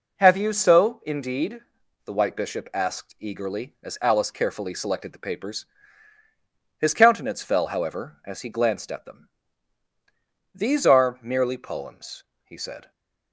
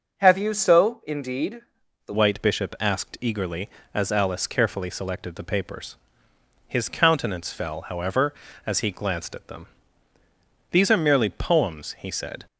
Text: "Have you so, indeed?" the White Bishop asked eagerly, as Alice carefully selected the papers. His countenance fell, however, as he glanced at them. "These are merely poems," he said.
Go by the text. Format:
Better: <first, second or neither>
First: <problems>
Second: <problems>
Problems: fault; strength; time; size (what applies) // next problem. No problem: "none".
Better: first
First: none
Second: changes voice at "White"; from 2.1 s on; 10.3 s long